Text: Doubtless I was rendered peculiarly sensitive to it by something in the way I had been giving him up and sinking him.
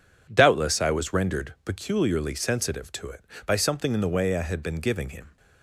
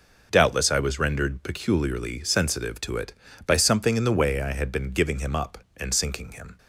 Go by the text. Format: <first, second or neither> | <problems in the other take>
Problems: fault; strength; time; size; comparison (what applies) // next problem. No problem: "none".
second | stops before "up and sinking him"; at 5.3 s